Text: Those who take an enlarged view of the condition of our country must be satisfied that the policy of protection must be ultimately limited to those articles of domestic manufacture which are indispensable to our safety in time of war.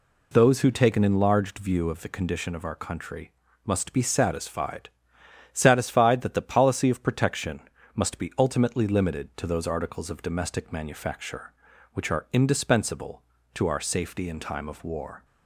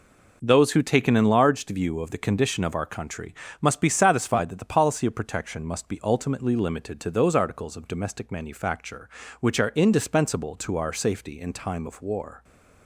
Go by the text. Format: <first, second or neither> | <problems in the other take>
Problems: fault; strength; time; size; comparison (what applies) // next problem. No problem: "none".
second | pauses between "country" and "must"; slight; at 3.3 s; 0.32 s long; slight in the second // says "satisfied" twice; at 5.5 s // pauses between "protection" and "must"; slight; at 7.6 s; 0.34 s long